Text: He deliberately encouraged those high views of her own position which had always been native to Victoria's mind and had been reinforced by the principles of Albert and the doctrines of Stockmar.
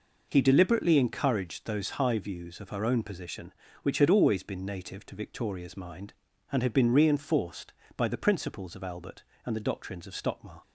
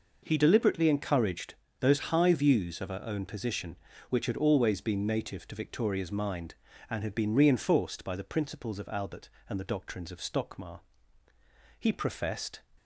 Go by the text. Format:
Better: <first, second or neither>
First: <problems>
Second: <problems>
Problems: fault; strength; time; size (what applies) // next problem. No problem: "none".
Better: first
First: none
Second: pauses between "encouraged" and "those"; slight; at 1.5 s; 0.28 s long // goes on to say "He professed"; noticeable; from 11.7 s on; 0.84 s long